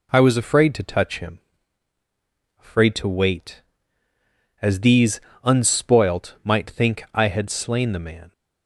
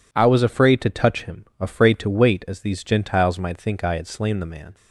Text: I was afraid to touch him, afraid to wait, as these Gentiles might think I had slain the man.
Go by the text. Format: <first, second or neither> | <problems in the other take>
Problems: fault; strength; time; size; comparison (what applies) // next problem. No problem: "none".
second | says "Unspoilt" for "Gentiles"; at 5.4 s